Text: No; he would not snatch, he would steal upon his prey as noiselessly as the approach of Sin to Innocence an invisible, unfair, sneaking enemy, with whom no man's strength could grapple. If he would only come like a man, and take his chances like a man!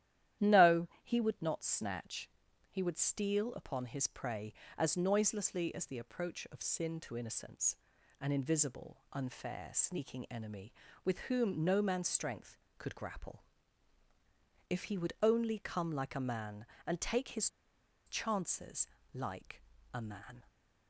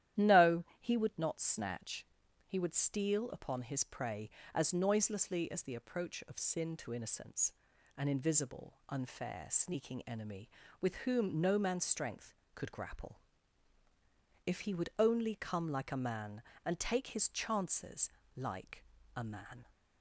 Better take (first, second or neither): second